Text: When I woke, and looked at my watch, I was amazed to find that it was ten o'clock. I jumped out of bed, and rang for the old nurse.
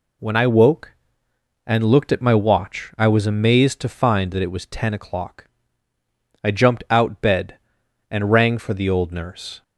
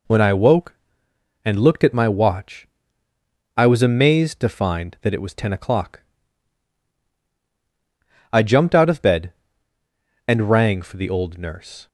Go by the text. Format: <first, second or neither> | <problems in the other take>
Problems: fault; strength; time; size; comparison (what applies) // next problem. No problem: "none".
second | skips "of"; at 7.2 s